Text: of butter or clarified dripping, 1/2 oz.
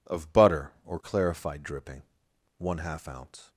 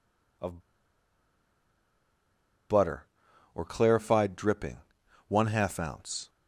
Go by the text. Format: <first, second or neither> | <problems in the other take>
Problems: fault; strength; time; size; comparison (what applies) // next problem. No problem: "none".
first | pauses between "of" and "butter"; strong; at 0.6 s; 2.0 s long